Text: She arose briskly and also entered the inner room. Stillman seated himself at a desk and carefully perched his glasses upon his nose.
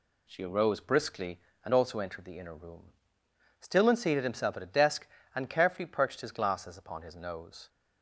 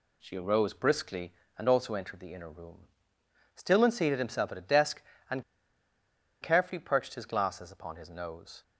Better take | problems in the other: first | pauses between "and" and "carefully"; at 5.4 s; 0.98 s long

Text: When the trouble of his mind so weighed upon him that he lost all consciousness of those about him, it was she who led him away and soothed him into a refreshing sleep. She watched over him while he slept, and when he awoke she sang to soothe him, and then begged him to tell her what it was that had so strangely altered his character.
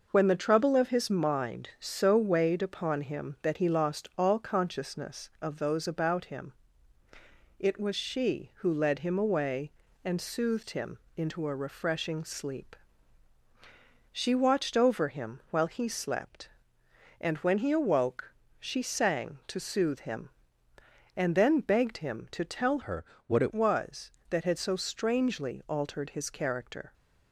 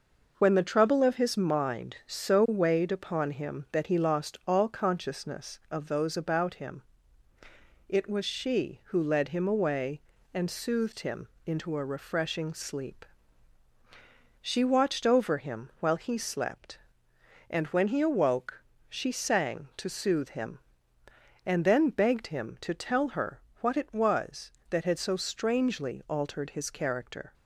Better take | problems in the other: second | pauses between "him" and "into"; slight; at 10.9 s; 0.20 s long; slight in the second // pauses between "awoke" and "she"; slight; at 18.3 s; 0.28 s long; slight in the second // changes voice from "her" to "it"; from 22.8 to 23.5 s; 0.7 s long // pauses between "her" and "what"; slight; at 23.0 s; 0.22 s long; slight in the second

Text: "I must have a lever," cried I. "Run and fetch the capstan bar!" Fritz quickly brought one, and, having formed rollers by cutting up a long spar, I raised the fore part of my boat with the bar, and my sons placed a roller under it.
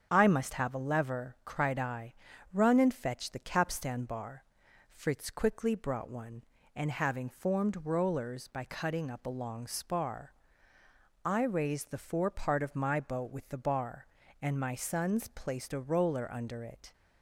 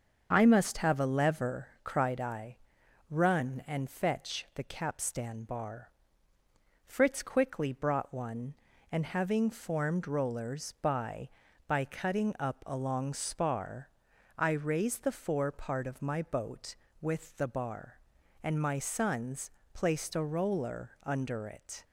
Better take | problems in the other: first | starts louder than the rest; until 1.3 s; 7 dB; strong in the first // says "by" twice; at 11.6 s // pauses between "sons" and "placed"; slight; at 19.5 s; 0.22 s long

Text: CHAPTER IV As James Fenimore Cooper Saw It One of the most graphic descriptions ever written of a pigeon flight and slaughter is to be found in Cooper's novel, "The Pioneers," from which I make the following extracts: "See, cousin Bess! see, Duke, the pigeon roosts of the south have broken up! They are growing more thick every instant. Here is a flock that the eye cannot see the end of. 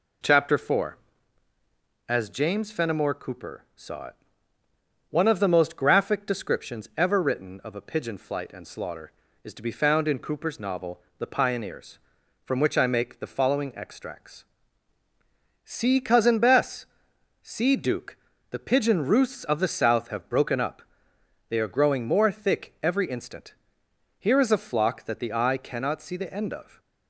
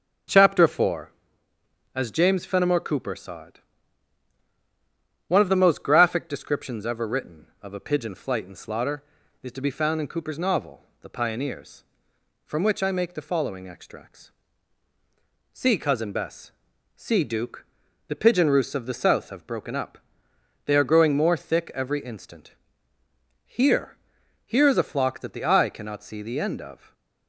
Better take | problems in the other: first | pauses between "It" and "One"; strong; at 3.6 s; 1.6 s long; noticeable in the first // says "Here" twice; at 24.4 s // stays silent after the last word; slight; from 26.7 s on; 0.5 s long

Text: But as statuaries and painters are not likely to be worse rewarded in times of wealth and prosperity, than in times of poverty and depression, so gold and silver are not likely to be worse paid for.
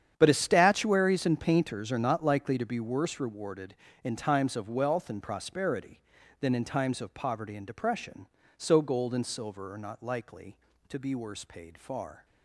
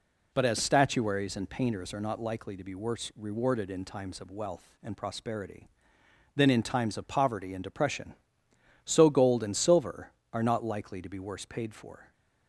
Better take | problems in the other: second | starts louder than the rest; strong; until 1.1 s; 9 dB // says "far" for "for"; at 11.7 s

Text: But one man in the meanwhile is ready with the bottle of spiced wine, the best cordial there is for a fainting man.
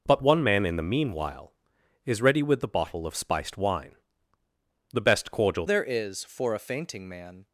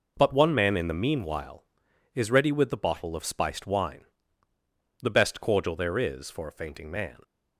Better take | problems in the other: second | changes voice at "there"; from 5.6 s on; 1.8 s long

